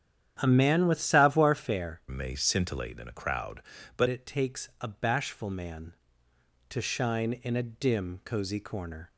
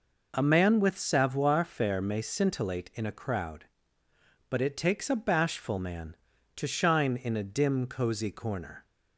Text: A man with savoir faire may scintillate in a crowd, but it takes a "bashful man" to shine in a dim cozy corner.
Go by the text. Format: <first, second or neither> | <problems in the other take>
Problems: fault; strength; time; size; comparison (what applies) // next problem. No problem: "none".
second | starts louder than the rest; strong; until 1.4 s; 9.5 dB // changes voice from "may" to "but"; from 2.0 to 4.0 s; 2.0 s long